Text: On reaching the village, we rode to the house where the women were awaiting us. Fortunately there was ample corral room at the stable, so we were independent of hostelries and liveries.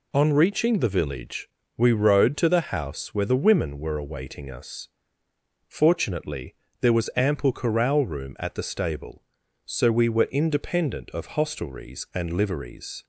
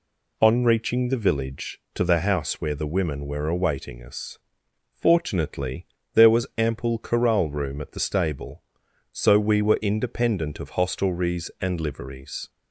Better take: first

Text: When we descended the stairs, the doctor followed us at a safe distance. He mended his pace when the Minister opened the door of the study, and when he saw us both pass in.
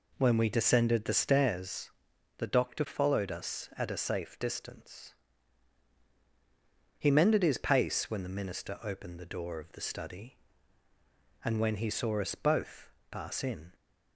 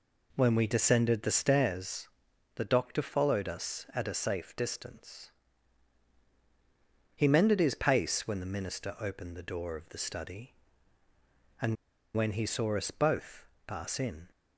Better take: first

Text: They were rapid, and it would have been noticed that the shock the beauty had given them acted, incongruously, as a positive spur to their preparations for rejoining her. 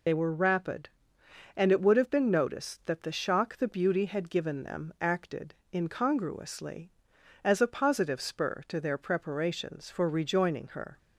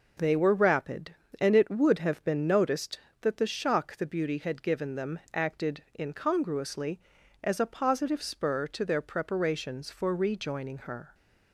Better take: second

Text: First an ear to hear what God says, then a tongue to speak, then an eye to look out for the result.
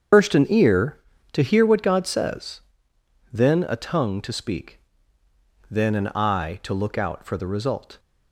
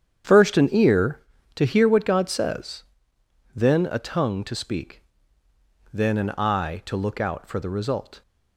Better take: second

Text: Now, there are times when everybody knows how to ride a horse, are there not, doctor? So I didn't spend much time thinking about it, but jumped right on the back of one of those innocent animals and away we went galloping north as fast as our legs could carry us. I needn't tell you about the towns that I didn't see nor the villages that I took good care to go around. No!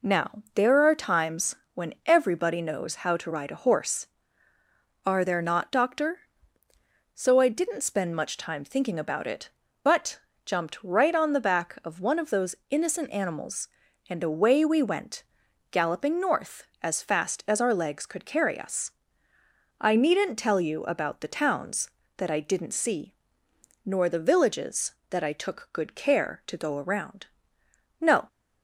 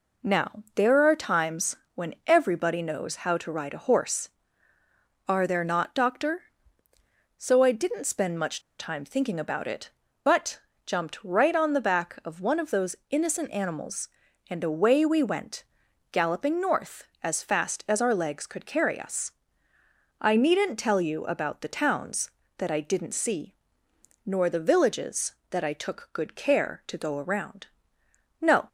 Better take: first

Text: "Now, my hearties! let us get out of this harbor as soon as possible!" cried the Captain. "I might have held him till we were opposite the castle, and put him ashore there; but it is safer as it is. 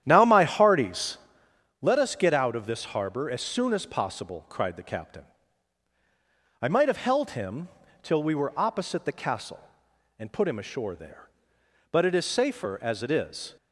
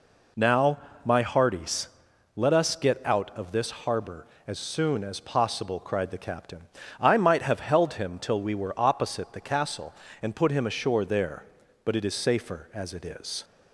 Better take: second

